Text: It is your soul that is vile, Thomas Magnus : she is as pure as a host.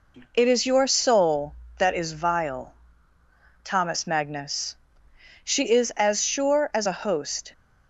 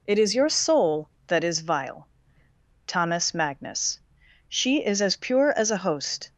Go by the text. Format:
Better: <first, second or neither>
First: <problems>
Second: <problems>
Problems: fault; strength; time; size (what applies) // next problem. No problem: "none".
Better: second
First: says "sure" for "pure"; at 6.2 s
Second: none